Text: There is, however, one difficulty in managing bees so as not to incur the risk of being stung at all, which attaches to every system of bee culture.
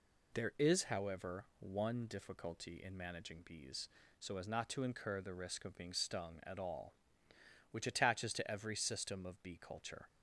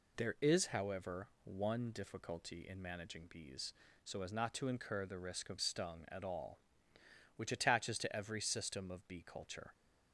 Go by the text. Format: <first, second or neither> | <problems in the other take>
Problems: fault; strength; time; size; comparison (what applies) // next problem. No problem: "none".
first | skips "being"; at 5.5 s